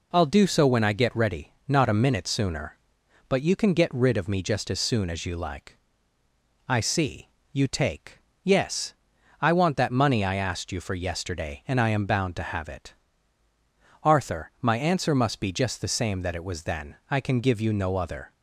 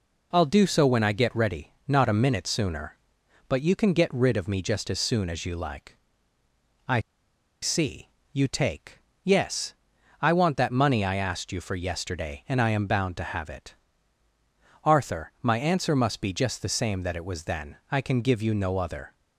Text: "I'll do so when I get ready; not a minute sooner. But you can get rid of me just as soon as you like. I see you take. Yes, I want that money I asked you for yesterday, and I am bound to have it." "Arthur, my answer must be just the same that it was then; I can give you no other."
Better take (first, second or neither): first